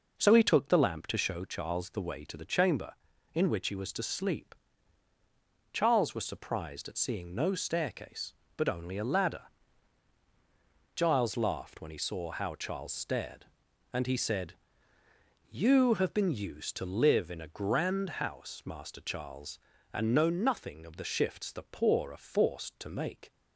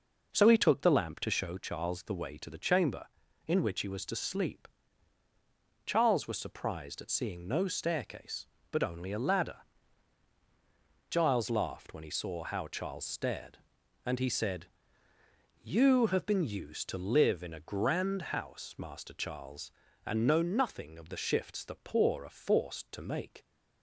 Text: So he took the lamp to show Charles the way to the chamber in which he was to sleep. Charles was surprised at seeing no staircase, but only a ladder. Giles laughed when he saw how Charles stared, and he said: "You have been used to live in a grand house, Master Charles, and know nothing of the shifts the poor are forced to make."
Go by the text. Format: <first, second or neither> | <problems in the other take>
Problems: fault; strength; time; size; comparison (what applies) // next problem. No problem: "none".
neither | none